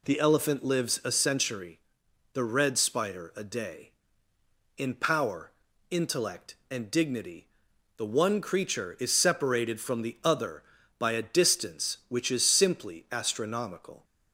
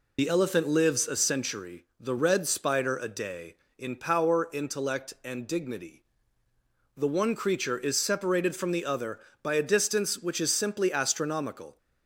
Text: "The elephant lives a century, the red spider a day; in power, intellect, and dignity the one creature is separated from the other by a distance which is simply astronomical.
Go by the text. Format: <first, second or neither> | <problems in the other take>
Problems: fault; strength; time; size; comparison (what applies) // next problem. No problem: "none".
first | loses the start of "The"; at 0.1 s; 65 ms // pauses between "dignity" and "the"; noticeable; at 6.0 s; 0.94 s long; noticeable in the first